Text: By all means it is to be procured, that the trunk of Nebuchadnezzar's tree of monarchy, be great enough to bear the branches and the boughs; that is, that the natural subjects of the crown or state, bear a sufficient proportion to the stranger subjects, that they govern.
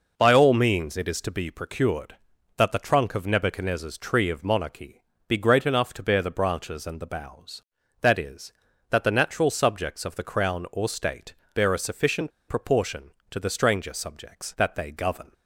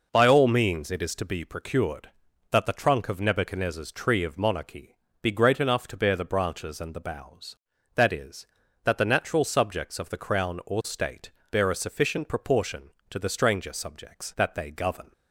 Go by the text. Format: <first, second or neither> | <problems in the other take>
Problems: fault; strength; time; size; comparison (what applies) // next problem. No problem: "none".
second | pauses between "sufficient" and "proportion"; slight; at 12.3 s; 0.17 s long